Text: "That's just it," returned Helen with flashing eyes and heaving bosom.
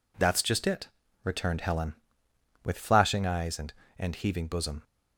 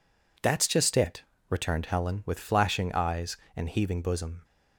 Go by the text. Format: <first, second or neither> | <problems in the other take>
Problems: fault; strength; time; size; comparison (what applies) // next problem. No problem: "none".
second | says "and" twice; at 3.9 s